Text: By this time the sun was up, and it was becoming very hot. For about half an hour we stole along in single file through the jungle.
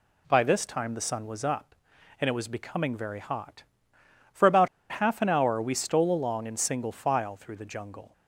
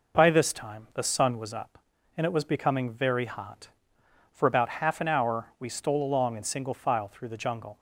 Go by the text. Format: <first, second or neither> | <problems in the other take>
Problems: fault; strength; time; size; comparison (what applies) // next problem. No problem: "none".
second | pauses between "about" and "half"; slight; at 4.6 s; 0.24 s long